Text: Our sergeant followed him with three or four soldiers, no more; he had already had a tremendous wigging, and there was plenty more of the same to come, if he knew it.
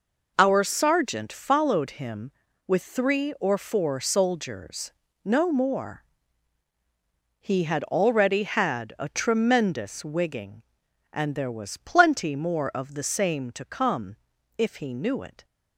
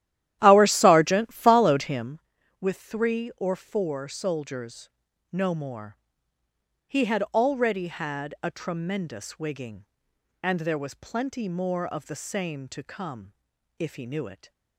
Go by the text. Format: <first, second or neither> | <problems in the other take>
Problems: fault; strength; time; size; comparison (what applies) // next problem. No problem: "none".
first | starts louder than the rest; strong; until 2.2 s; 12.5 dB